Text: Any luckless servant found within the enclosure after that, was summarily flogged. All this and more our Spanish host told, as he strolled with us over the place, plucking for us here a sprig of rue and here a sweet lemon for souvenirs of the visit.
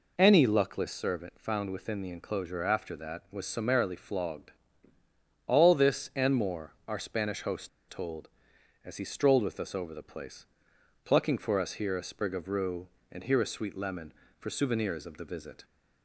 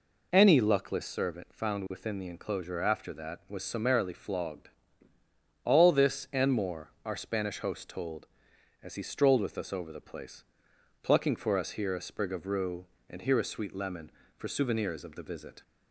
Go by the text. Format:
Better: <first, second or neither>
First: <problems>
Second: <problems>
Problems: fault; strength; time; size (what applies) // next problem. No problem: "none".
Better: second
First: pauses between "host" and "told"; slight; at 7.6 s; 0.21 s long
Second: none